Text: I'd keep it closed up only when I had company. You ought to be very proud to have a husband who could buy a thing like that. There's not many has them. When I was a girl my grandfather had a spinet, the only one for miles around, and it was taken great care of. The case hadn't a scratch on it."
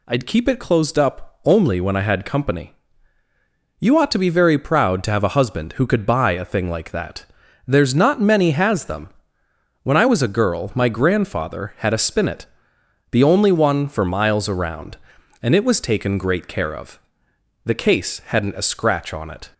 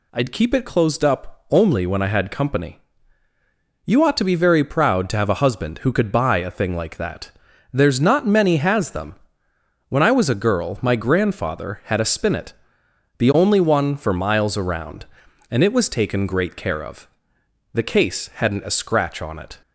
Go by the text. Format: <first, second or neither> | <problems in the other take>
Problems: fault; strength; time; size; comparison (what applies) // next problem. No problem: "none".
neither | none